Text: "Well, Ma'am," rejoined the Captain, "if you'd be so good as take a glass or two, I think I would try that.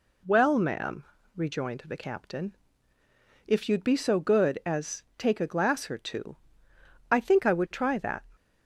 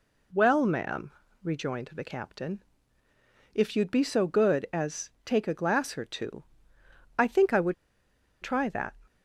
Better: first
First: none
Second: pauses between "would" and "try"; noticeable; at 7.7 s; 0.66 s long

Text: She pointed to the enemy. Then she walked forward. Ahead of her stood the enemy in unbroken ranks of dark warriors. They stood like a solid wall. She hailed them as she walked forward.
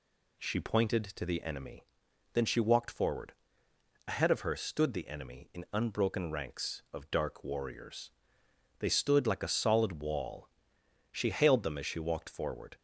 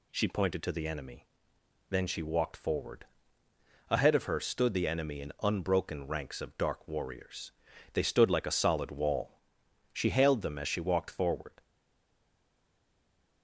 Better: first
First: none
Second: stays silent after the last word; noticeable; from 11.6 s on; 1.8 s long

